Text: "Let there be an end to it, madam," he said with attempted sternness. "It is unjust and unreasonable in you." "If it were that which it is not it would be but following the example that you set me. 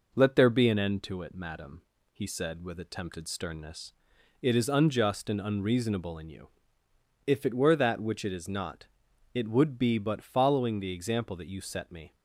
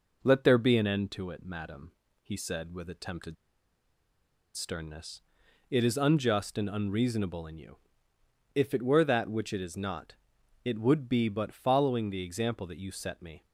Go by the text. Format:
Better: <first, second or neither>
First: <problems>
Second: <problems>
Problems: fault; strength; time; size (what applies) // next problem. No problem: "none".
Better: first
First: pauses between "not" and "it"; noticeable; at 8.8 s; 0.48 s long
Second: pauses between "attempted" and "sternness"; at 3.3 s; 1.2 s long // pauses between "not" and "it"; noticeable; at 10.1 s; 0.50 s long